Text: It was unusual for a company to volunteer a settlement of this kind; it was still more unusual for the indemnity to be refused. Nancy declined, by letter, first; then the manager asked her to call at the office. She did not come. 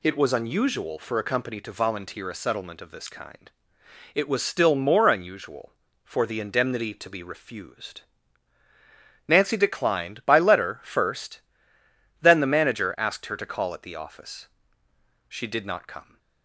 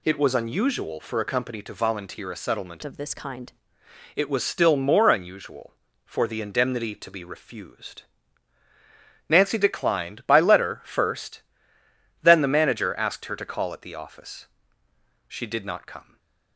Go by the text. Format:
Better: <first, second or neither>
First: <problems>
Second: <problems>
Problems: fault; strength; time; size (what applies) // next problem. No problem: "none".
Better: first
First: none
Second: changes voice from "of" to "kind"; from 2.8 to 3.5 s; 0.7 s long // stays silent after the last word; slight; from 16.0 s on; 0.5 s long